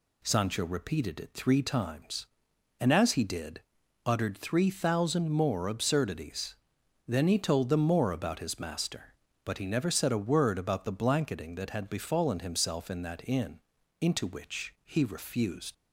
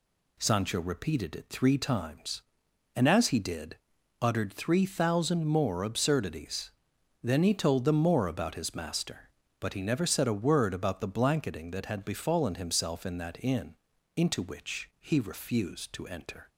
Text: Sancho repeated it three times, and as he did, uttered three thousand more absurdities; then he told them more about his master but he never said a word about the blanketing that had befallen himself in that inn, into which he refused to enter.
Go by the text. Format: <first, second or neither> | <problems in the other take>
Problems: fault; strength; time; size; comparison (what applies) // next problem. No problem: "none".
second | stops before "to enter"; at 15.7 s